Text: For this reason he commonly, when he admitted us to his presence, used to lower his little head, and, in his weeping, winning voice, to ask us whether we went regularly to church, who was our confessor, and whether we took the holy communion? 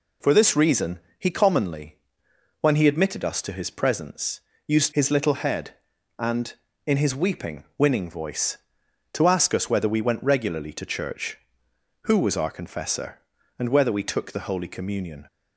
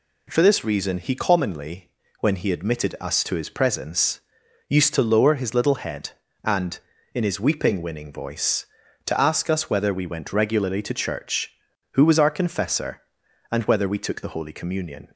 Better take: second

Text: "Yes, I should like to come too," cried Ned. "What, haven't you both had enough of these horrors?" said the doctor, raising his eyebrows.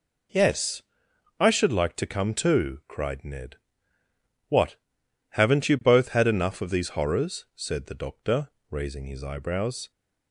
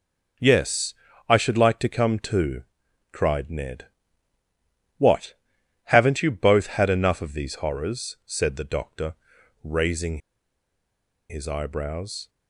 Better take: first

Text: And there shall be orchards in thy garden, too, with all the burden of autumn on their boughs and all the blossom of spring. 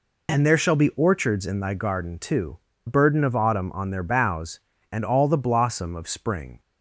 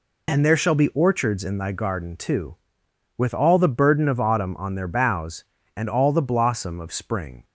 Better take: second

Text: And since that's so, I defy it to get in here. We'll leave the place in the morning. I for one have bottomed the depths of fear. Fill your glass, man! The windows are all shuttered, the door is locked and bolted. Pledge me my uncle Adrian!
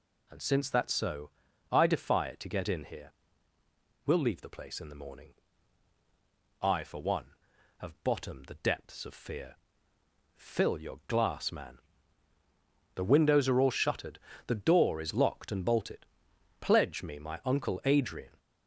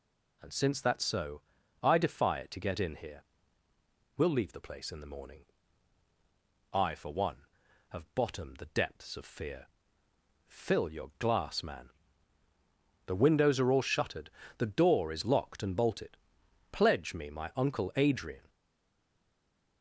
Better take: first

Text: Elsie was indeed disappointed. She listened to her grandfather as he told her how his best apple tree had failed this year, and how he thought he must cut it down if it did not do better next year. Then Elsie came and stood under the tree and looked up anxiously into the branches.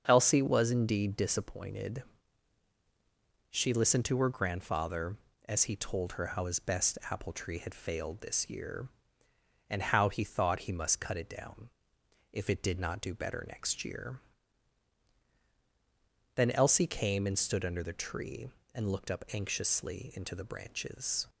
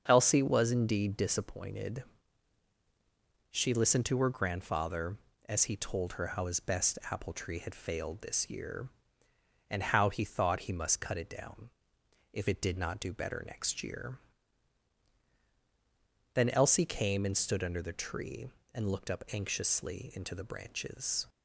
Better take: neither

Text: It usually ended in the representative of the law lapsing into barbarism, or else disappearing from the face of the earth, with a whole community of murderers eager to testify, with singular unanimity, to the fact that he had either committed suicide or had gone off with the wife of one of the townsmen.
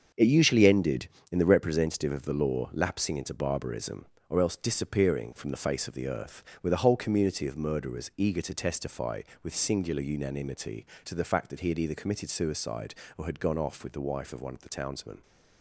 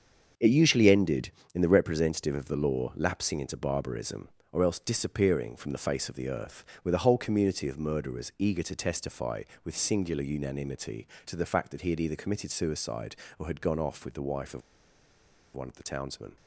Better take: first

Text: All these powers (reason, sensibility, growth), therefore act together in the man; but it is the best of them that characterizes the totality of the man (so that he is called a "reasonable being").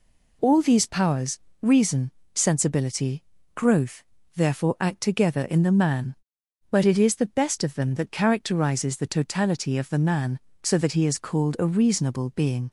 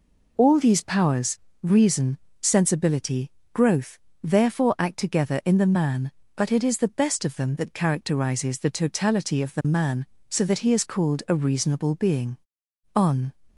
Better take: first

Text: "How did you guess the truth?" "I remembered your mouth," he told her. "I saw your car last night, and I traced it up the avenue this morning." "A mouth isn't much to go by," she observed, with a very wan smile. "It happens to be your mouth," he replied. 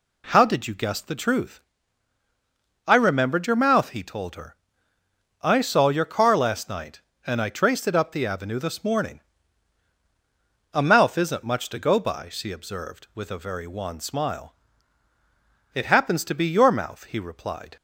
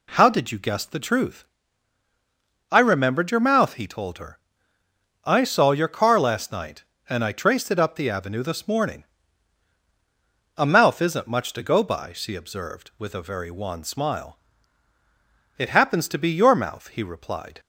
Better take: neither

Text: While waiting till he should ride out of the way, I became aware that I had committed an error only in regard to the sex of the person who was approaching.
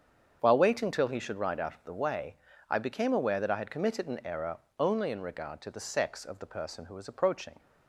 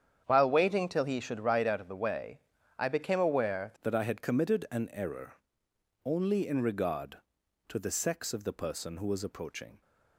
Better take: first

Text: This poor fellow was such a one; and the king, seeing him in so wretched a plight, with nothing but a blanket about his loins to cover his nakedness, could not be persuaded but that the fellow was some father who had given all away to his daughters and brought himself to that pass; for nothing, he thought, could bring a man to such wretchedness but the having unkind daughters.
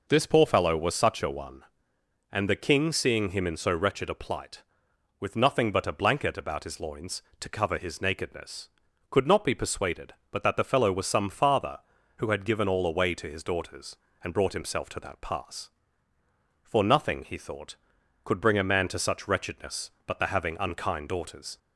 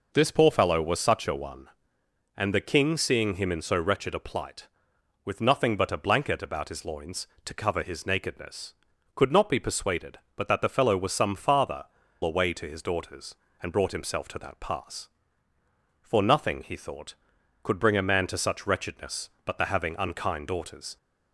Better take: first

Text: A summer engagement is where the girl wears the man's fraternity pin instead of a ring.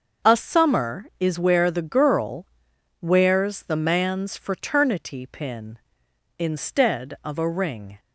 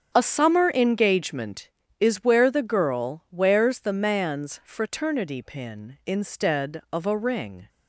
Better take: second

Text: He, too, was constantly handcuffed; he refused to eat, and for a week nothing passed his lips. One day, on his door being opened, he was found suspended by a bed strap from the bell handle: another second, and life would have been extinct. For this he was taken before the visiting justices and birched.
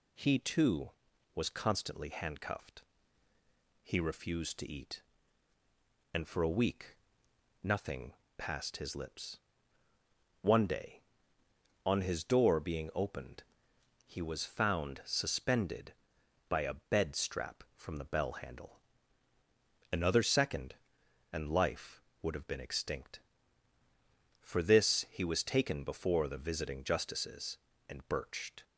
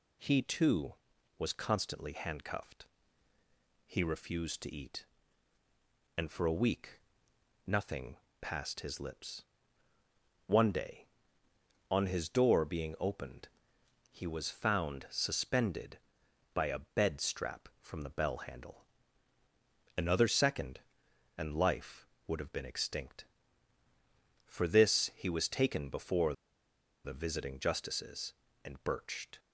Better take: first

